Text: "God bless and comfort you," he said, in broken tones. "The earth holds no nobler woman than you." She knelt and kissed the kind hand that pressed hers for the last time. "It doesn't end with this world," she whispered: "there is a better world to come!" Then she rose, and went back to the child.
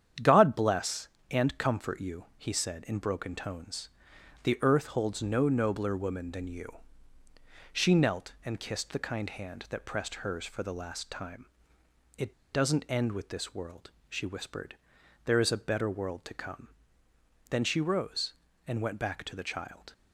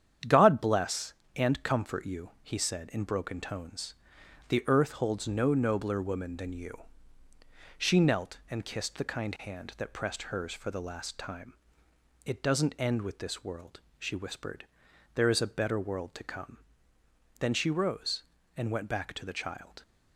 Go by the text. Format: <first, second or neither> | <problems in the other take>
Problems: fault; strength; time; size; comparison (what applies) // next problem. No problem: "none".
second | starts louder than the rest; strong; until 1.4 s; 9 dB; strong in the second // pauses between "It" and "doesn't"; slight; at 12.3 s; 0.20 s long